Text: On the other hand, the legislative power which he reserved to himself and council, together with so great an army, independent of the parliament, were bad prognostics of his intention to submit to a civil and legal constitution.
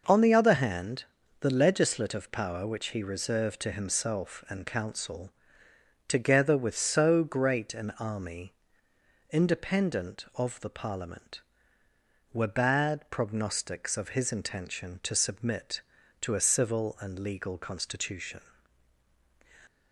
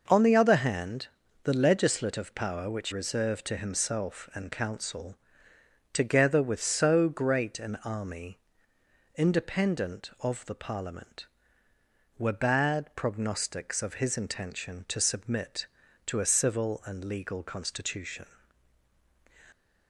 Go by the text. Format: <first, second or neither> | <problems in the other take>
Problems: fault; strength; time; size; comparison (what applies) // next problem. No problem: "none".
first | skips "he"; at 2.9 s